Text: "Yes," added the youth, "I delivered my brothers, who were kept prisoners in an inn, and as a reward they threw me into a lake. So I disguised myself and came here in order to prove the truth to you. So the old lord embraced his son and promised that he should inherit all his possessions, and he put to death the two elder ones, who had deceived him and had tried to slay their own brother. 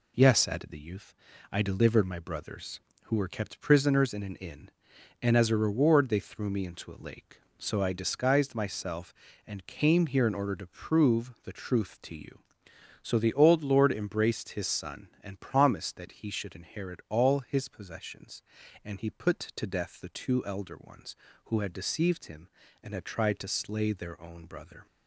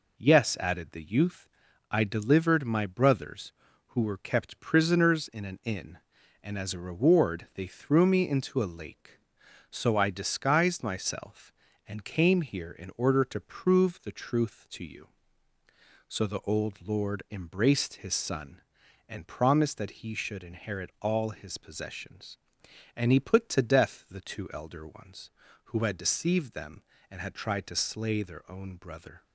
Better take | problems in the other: first | says "them" for "him"; at 26.5 s

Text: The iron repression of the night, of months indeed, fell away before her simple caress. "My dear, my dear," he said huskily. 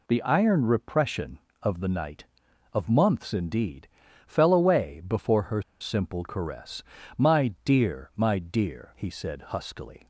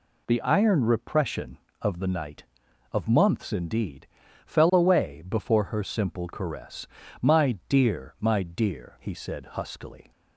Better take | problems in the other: second | pauses between "her" and "simple"; slight; at 5.6 s; 0.18 s long

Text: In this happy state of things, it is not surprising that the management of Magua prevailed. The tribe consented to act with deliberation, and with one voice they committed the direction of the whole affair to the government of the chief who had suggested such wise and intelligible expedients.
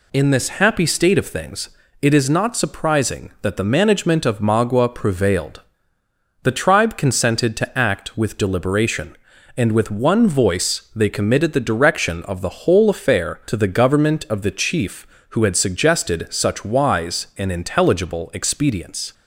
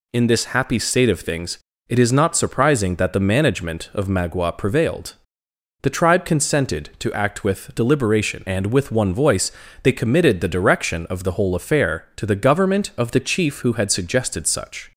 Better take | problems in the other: first | pauses between "voice" and "they"; slight; at 9.5 s; 0.32 s long // stops before "wise and intelligible expedients"; at 14.9 s

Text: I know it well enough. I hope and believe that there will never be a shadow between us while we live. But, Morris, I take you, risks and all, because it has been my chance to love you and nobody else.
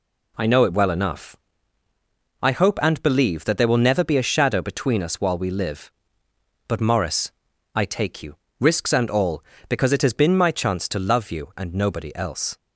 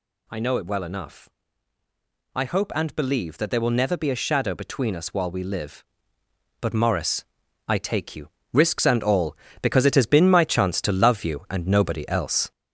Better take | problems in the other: first | gets louder; noticeable; throughout; 5.5 dB

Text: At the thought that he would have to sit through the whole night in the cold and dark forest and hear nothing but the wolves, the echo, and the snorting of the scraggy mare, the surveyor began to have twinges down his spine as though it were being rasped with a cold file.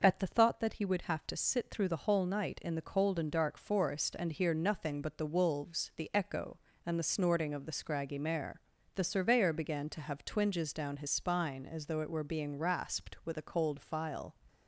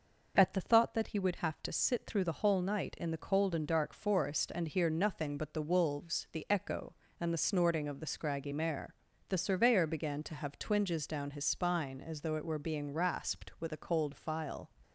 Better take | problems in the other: neither | none

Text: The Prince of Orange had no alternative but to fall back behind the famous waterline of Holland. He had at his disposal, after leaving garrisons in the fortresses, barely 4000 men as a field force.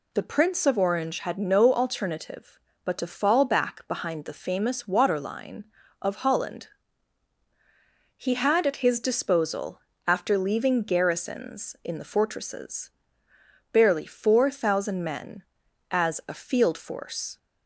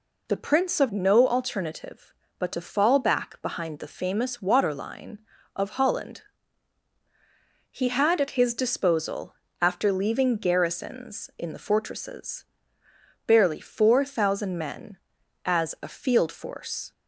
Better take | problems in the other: first | skips "Orange had"; at 0.9 s

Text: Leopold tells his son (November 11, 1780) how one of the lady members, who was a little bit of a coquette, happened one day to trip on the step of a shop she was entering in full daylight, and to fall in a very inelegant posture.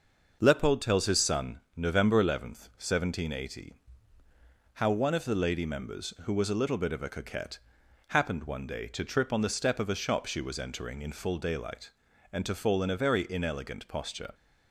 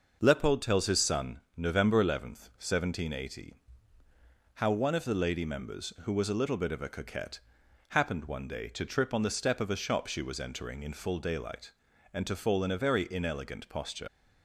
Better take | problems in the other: first | leaves "posture" unfinished; at 14.0 s; 75 ms

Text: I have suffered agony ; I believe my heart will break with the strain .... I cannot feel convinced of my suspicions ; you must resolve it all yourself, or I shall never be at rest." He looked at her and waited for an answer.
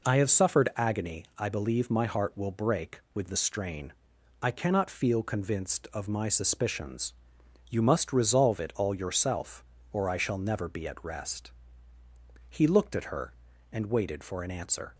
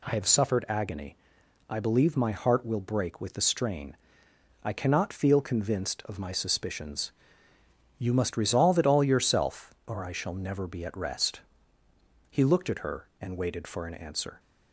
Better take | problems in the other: neither | none

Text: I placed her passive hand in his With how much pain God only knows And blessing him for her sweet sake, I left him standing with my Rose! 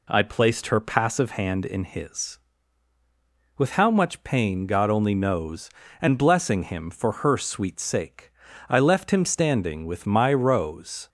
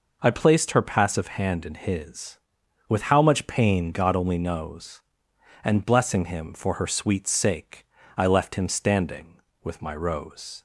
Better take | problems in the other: neither | none

